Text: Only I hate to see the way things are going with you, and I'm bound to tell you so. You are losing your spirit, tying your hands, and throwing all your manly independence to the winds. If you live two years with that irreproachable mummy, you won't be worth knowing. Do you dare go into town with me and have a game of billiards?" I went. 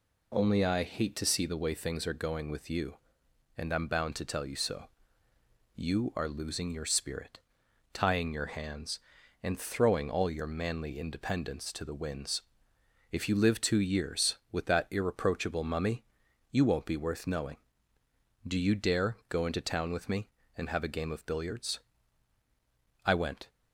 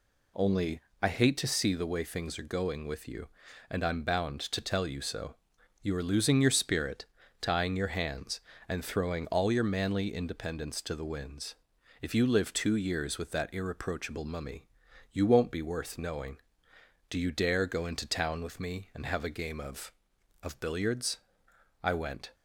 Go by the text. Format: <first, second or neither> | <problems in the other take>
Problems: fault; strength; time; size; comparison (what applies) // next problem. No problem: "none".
first | pauses between "Only" and "I"; slight; at 0.7 s; 0.22 s long // says "of" twice; at 20.4 s